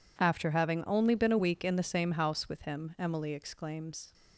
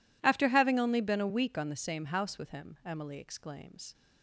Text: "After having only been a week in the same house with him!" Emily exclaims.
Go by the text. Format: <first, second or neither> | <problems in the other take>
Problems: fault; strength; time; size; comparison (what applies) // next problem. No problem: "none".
first | says "on" for "in"; at 1.5 s